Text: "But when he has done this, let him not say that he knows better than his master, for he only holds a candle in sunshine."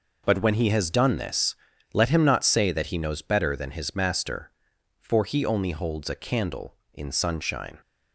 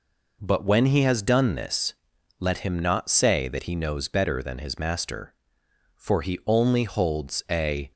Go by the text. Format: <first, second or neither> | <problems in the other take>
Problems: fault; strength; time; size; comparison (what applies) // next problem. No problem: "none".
first | stops before "candle in sunshine"; at 7.9 s